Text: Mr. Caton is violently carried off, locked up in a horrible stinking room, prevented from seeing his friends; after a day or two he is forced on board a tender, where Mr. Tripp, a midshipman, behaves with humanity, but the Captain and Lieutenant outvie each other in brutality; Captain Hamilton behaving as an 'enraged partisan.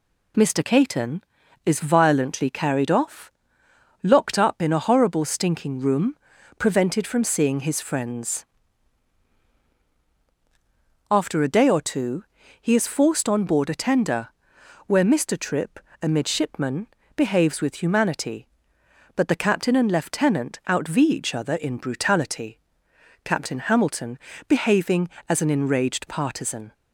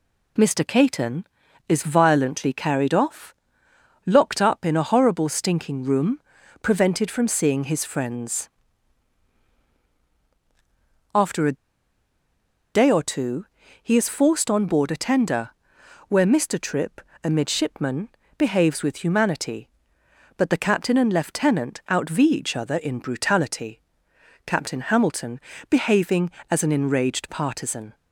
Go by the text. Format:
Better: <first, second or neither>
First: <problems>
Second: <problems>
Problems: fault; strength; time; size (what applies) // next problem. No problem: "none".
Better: first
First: pauses between "two" and "he"; slight; at 12.2 s; 0.36 s long // pauses between "Hamilton" and "behaving"; slight; at 24.1 s; 0.32 s long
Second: pauses between "a" and "day"; at 11.5 s; 1.1 s long // pauses between "two" and "he"; slight; at 13.4 s; 0.36 s long // pauses between "Hamilton" and "behaving"; slight; at 25.3 s; 0.32 s long